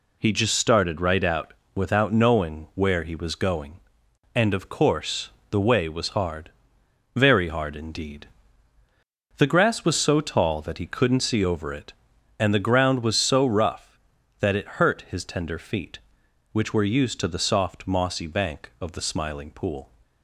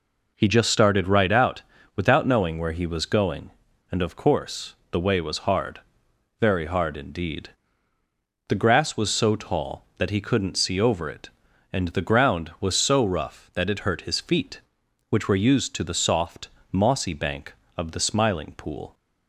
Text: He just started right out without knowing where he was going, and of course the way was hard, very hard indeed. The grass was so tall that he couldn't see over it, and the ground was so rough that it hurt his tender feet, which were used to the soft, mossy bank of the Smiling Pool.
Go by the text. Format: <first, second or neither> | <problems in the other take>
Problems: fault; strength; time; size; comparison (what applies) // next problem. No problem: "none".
first | pauses between "out" and "without"; slight; at 1.6 s; 0.34 s long; slight in the first // pauses between "course" and "the"; slight; at 4.7 s; 0.16 s long; slight in the first // skips "tender"; at 14.1 s